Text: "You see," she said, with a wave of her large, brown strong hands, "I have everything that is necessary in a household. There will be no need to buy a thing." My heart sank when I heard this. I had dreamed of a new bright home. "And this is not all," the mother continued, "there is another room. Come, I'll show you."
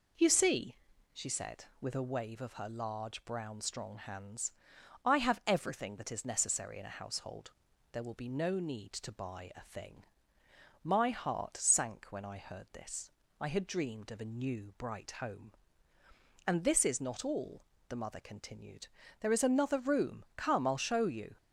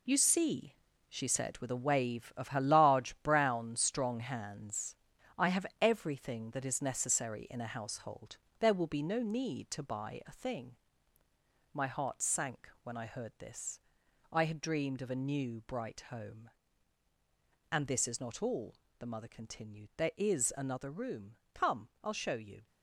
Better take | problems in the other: first | gets quieter; strong; throughout; 9 dB

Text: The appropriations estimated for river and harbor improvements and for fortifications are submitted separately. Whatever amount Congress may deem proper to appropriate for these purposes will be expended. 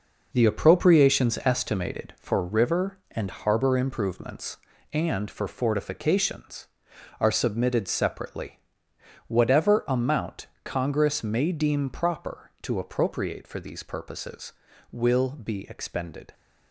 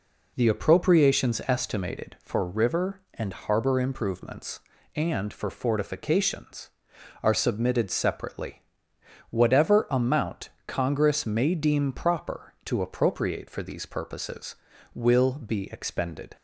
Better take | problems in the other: second | gets quieter; strong; throughout; 8 dB // pauses between "amount" and "Congress"; slight; at 10.4 s; 0.16 s long; slight in the second

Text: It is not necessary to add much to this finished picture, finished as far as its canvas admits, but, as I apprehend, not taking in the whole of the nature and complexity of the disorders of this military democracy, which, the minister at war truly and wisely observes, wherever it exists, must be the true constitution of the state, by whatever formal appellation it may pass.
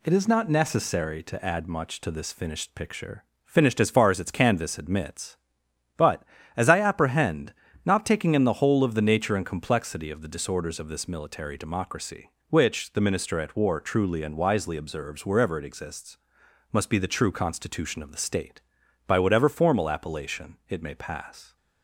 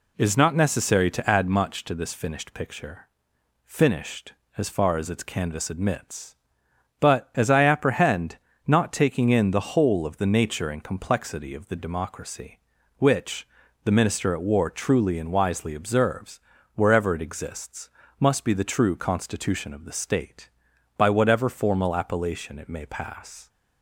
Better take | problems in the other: first | skips "disorders of this military"; at 11.7 s

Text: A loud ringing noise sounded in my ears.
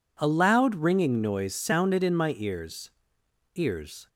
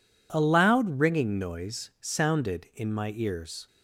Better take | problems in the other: second | says "ears" twice; at 3.5 s

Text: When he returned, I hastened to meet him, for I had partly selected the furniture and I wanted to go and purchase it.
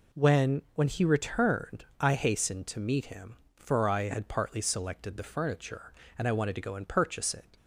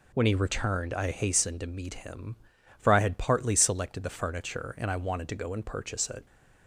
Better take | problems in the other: second | says "When" twice; at 0.7 s

